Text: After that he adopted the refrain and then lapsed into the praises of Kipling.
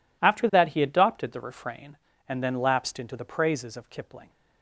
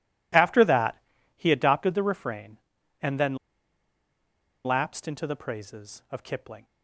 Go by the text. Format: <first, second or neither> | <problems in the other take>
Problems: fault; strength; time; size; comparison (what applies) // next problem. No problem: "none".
first | pauses between "that" and "he"; slight; at 0.9 s; 0.36 s long // pauses between "then" and "lapsed"; strong; at 3.3 s; 1.2 s long